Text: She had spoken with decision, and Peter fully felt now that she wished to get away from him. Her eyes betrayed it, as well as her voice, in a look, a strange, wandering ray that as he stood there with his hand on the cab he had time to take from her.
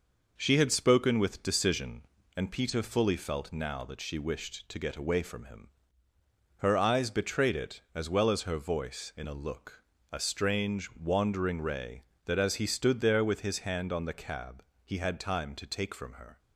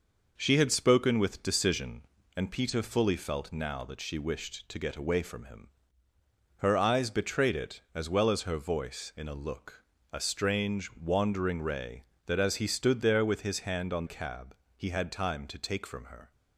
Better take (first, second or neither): first